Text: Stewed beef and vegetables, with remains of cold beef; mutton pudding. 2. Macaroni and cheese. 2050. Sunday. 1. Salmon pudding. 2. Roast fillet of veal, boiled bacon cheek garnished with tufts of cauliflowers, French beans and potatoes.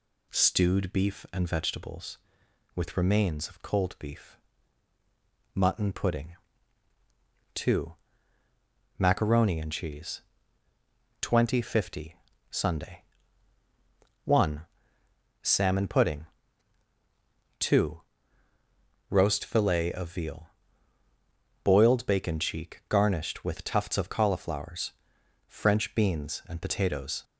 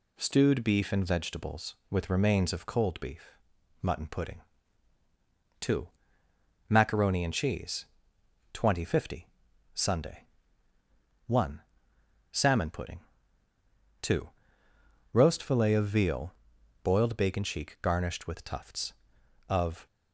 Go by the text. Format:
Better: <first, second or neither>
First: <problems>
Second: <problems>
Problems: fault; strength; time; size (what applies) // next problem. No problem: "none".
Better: first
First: none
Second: stops before "cauliflowers French beans and potatoes"; at 19.8 s